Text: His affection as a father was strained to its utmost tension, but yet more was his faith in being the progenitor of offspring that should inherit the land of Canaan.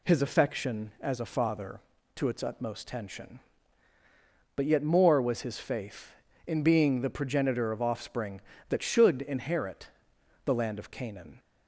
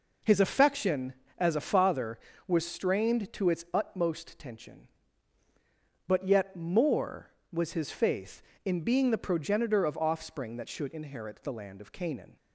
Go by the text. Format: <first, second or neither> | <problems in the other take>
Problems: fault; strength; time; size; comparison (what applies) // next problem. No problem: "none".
second | skips "was strained"; at 1.9 s // pauses between "inherit" and "the"; noticeable; at 9.8 s; 0.58 s long